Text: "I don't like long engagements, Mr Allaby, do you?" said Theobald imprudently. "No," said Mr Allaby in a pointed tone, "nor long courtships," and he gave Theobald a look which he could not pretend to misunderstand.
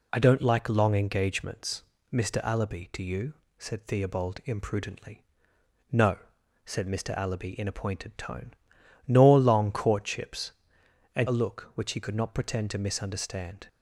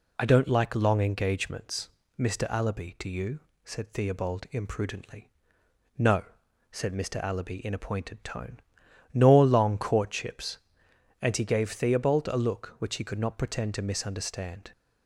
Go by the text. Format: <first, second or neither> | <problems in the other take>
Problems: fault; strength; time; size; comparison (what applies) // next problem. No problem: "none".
second | skips "he gave Theobald"; at 11.2 s